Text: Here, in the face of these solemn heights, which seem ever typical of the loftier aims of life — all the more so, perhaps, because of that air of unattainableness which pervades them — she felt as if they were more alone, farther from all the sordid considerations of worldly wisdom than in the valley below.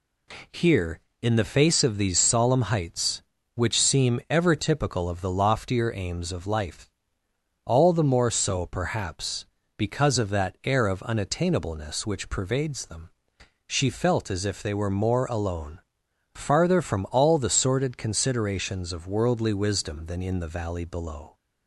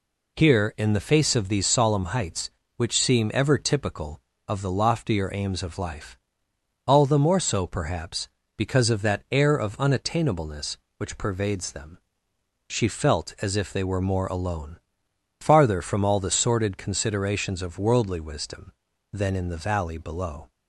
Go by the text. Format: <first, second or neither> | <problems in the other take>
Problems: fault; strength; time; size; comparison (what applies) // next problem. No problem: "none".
neither | none